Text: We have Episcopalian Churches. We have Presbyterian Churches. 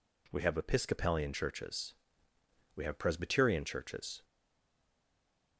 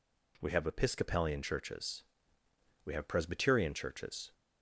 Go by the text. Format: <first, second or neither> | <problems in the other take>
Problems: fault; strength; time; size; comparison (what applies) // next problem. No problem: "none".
second | stays silent after the last word; noticeable; from 4.2 s on; 1.3 s long